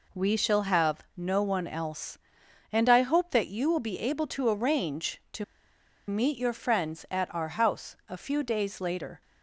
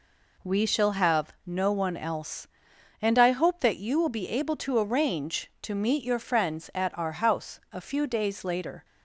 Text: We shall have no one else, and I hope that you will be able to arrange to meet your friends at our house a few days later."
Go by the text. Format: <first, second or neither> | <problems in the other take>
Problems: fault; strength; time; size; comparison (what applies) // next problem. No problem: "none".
second | pauses between "to" and "meet"; noticeable; at 5.4 s; 0.64 s long